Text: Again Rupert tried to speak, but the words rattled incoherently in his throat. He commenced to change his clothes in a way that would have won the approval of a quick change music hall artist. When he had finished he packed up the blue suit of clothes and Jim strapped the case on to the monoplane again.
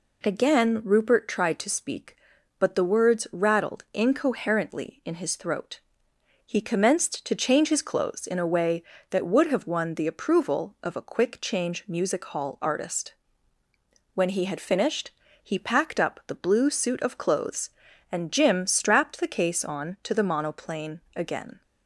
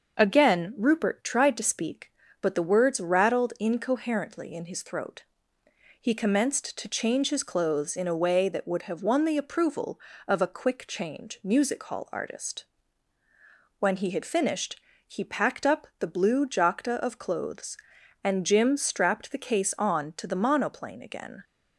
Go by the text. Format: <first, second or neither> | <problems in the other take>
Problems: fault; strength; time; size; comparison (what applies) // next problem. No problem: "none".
first | starts louder than the rest; until 1.1 s; 6.5 dB // pauses between "finished" and "he"; slight; at 14.7 s; 0.28 s long; slight in the first // says "jacta" for "suit"; at 16.4 s